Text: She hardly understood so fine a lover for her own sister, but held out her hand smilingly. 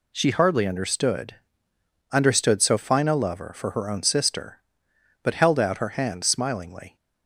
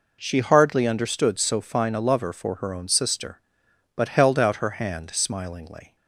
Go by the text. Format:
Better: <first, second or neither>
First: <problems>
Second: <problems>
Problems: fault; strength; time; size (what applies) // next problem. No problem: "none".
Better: second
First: says "understood" twice; at 2.1 s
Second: none